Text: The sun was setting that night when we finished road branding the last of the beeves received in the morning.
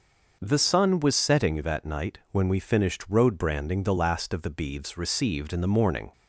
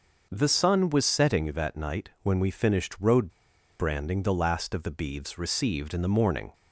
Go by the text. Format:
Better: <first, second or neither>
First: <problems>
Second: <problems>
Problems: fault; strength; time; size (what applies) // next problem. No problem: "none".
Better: first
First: starts louder than the rest; noticeable; until 1.4 s; 6 dB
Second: starts louder than the rest; noticeable; until 1.3 s; 6 dB // pauses between "road" and "branding"; noticeable; at 3.3 s; 0.48 s long